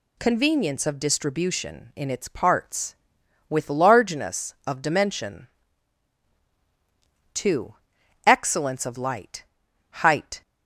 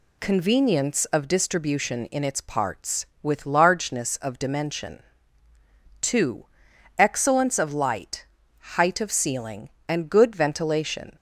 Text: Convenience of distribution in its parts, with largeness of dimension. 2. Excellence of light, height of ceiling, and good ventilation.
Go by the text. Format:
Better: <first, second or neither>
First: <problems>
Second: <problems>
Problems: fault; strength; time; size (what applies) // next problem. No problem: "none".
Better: second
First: stops before "of ceiling and good ventilation"; at 10.4 s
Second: none